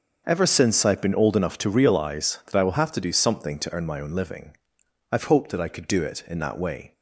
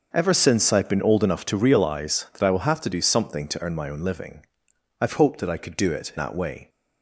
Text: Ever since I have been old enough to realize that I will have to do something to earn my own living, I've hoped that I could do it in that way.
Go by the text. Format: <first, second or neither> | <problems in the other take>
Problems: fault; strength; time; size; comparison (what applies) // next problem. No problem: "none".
first | starts louder than the rest; until 1.1 s; 6.5 dB; also in the first // skips "in"; at 6.1 s